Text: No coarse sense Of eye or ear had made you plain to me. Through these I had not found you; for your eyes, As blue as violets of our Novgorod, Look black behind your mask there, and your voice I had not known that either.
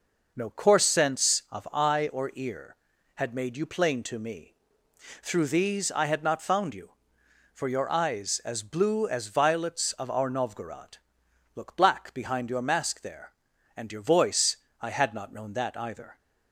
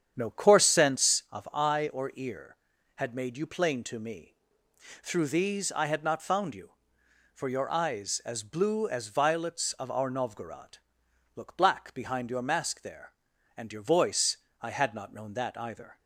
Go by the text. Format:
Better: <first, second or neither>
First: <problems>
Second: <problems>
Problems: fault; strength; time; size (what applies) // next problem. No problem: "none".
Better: first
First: pauses between "voice" and "I"; slight; at 14.5 s; 0.26 s long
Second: starts louder than the rest; strong; until 1.2 s; 8.5 dB // pauses between "voice" and "I"; slight; at 14.3 s; 0.26 s long